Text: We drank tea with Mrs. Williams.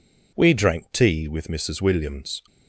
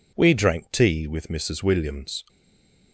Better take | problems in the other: first | stays silent after the last word; slight; from 2.2 s on; 0.7 s long

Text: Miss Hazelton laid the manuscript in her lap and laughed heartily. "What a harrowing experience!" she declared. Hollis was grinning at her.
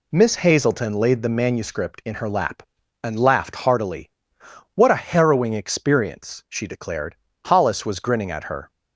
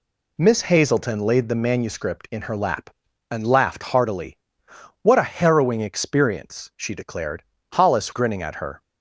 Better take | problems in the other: first | skips "was"; at 8.1 s

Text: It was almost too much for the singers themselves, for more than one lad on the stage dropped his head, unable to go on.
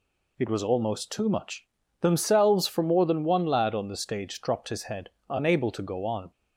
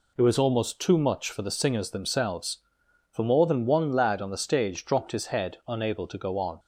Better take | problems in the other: second | skips "for the singers"; at 1.8 s

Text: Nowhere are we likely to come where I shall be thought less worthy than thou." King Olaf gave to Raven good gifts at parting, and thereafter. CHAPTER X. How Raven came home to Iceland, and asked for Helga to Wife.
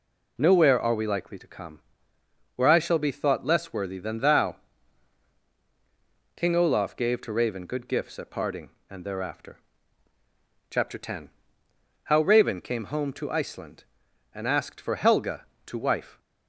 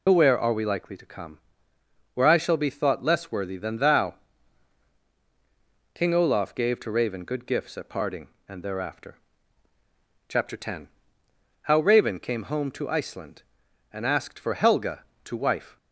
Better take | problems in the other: first | loses the start of "Nowhere"; at 0.0 s; 100 ms // pauses between "come" and "where"; noticeable; at 1.3 s; 0.74 s long; noticeable in the first

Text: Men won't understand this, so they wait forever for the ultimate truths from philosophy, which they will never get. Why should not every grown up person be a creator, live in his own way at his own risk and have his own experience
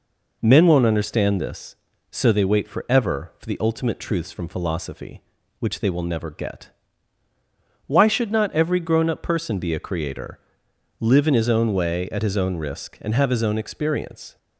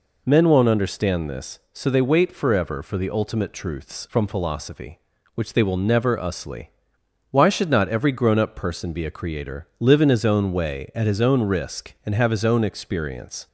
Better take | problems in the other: first | says "usly" for "get"; at 6.1 s

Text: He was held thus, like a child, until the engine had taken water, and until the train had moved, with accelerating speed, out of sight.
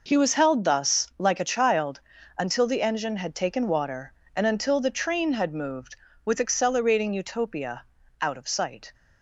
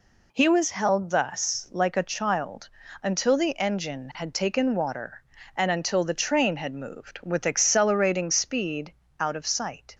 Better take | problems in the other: second | says "utopia" for "speed"; at 7.1 s

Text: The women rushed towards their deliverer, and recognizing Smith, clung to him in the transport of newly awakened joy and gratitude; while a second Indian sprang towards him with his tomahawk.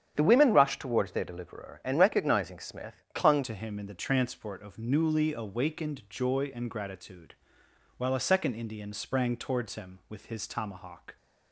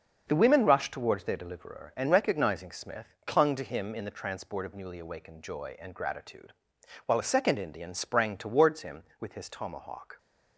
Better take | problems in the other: second | starts louder than the rest; strong; until 1.1 s; 9 dB; also in the second // changes voice at "to"; from 3.4 s on; 7.7 s long

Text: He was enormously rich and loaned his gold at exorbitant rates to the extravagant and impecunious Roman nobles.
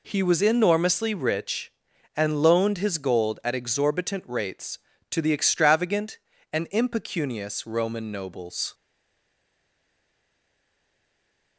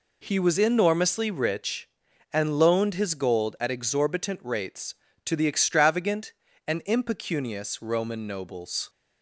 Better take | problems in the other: second | stays silent after the last word; strong; from 8.7 s on; 2.8 s long

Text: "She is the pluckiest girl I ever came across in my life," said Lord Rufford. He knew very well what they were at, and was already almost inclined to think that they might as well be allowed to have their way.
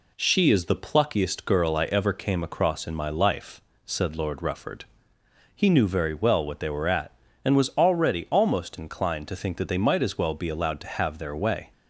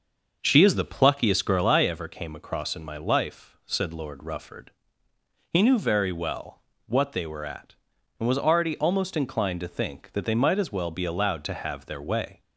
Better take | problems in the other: first | starts louder than the rest; until 1.7 s; 6 dB // pauses between "well" and "what"; slight; at 6.6 s; 0.24 s long

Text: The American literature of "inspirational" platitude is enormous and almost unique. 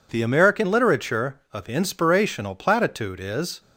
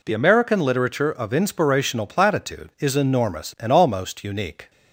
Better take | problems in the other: second | stops before "enormous and almost unique"; at 3.6 s

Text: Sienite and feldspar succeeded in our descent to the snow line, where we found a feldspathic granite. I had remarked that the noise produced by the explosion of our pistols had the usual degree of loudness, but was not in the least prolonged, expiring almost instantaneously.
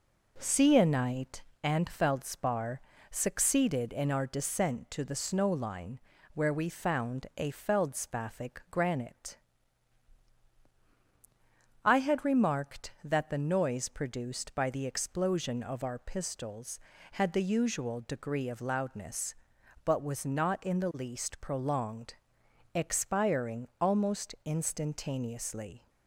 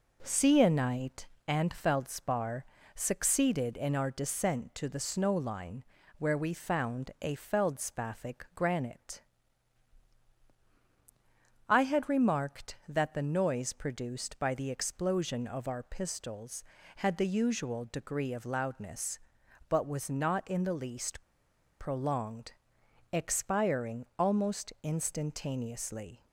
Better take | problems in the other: first | pauses between "feldspar" and "succeeded"; slight; at 2.6 s; 0.30 s long; slight in the first // pauses between "least" and "prolonged"; noticeable; at 21.2 s; 0.56 s long

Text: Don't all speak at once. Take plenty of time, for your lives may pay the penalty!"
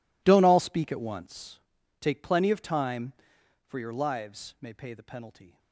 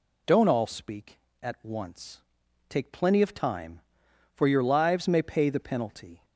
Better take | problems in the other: second | gets quieter; strong; throughout; 20 dB

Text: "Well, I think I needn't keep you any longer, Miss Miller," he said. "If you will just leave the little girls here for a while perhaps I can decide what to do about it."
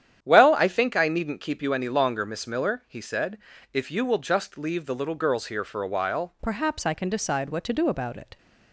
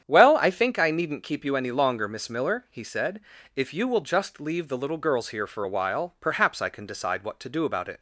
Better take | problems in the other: second | starts louder than the rest; strong; until 1.2 s; 10 dB; strong in the second // changes voice at "perhaps"; from 6.4 s on; 1.9 s long

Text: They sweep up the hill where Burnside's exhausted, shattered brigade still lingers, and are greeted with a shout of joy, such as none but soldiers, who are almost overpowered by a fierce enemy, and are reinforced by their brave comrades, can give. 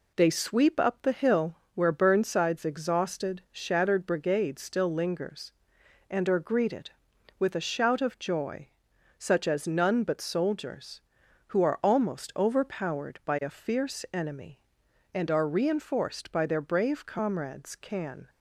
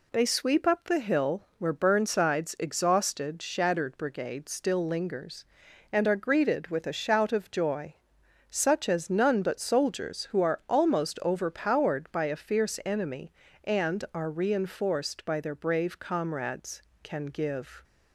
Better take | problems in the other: second | pauses between "hill" and "where"; slight; at 1.5 s; 0.20 s long // stops before "give"; at 18.2 s

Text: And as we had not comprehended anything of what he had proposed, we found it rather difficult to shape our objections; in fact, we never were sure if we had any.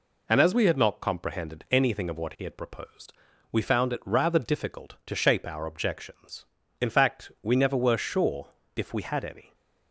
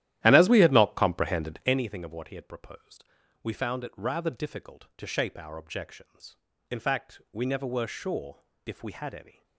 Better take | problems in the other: first | starts louder than the rest; strong; until 1.8 s; 13 dB // pauses between "sure" and "if"; slight; at 8.3 s; 0.26 s long; slight in the first

